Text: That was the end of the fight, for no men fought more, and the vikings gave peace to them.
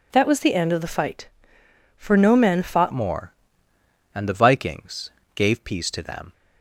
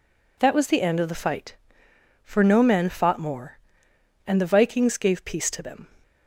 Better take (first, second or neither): second